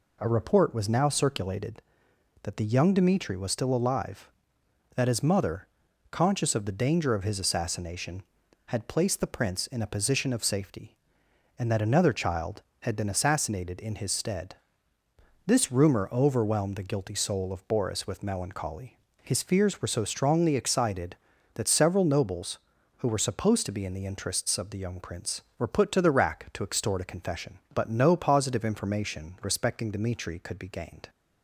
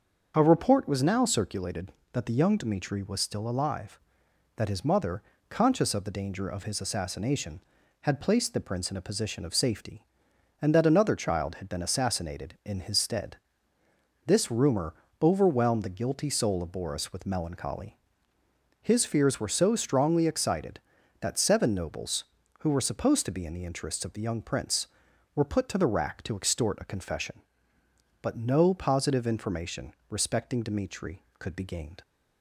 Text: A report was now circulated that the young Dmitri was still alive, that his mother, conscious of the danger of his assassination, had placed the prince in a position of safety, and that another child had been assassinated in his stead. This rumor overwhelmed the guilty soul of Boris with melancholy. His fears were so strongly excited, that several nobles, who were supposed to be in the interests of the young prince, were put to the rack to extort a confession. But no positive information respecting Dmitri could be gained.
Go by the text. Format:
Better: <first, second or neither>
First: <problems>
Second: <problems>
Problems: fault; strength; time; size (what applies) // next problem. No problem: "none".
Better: first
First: none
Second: starts louder than the rest; until 1.3 s; 6.5 dB // pauses between "rumor" and "overwhelmed"; slight; at 14.9 s; 0.28 s long // says "seven" for "several"; at 21.3 s // pauses between "information" and "respecting"; slight; at 29.9 s; 0.16 s long